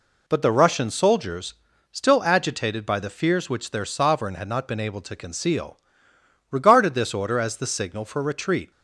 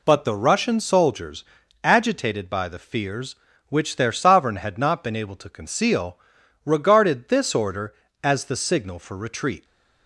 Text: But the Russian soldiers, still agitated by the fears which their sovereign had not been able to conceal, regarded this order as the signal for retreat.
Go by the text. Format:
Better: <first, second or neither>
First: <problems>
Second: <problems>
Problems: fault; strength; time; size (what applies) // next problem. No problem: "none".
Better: first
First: none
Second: skips "still"; at 1.6 s